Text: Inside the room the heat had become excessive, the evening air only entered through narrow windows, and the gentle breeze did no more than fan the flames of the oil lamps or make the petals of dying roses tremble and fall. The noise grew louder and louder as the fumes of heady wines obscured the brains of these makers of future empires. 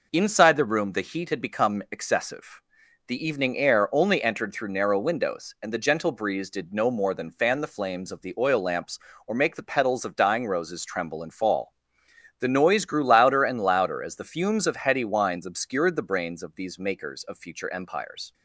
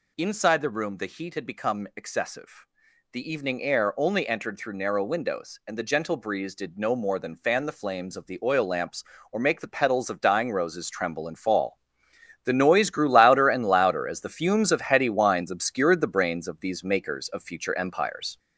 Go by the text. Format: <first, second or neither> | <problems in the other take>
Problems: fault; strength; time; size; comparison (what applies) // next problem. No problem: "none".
first | gets louder; noticeable; throughout; 4.5 dB